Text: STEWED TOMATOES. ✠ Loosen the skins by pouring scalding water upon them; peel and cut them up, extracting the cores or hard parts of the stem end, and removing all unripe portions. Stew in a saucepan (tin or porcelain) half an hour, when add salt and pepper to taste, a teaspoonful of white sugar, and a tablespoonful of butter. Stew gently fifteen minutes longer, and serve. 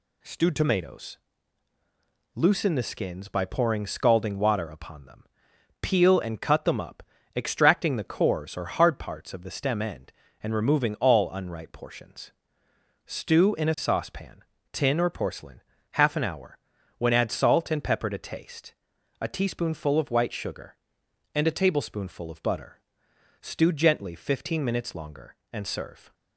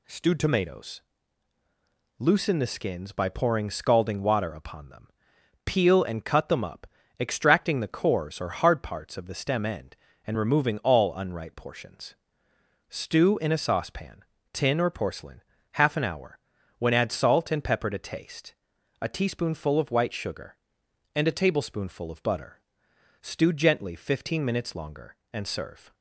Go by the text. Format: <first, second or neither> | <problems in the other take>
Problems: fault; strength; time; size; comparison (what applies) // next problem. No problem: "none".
neither | none